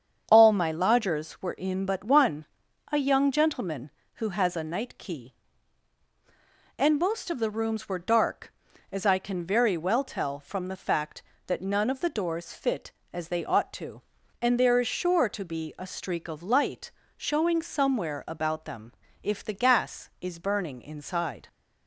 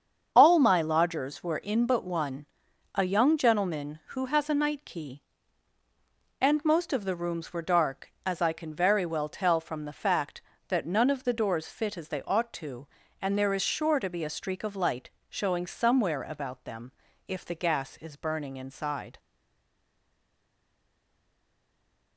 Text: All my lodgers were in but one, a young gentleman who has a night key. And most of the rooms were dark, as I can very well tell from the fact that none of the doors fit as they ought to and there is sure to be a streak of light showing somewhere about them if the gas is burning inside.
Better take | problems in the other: first | starts louder than the rest; strong; until 1.3 s; 7 dB; strong in the first // pauses between "light" and "showing"; slight; at 15.1 s; 0.18 s long; slight in the first // pauses between "them" and "if"; slight; at 16.9 s; 0.36 s long; slight in the first // stays silent after the last word; strong; from 19.1 s on; 3.0 s long

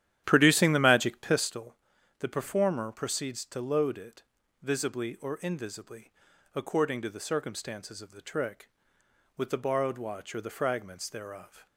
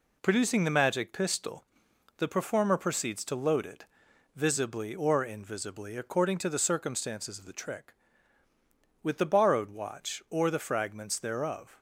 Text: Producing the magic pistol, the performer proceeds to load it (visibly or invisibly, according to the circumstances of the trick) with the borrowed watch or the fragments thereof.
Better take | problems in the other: second | starts louder than the rest; strong; until 1.5 s; 11.5 dB

